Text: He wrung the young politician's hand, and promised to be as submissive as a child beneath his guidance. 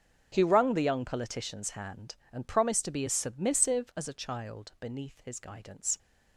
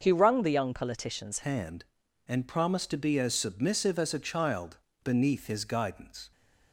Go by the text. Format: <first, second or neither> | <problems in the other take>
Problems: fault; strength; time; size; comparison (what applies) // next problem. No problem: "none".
first | starts louder than the rest; until 1.0 s; 6.5 dB; strong in the first // changes voice at "hand"; from 1.4 s on; 4.9 s long // pauses between "child" and "beneath"; slight; at 4.7 s; 0.24 s long